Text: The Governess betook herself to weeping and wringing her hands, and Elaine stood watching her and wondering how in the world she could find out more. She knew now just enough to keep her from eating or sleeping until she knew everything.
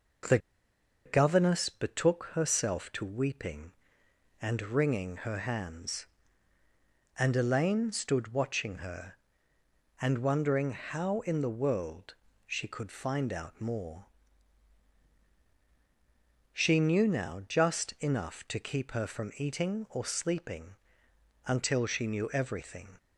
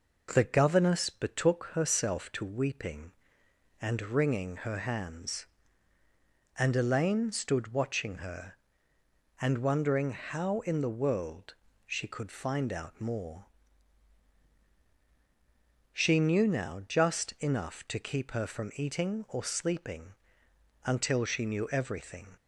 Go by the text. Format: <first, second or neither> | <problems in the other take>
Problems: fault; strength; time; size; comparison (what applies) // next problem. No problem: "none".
second | pauses between "The" and "Governess"; noticeable; at 0.3 s; 0.67 s long // pauses between "world" and "she"; slight; at 12.1 s; 0.32 s long; slight in the second // pauses between "sleeping" and "until"; noticeable; at 20.7 s; 0.74 s long; noticeable in the second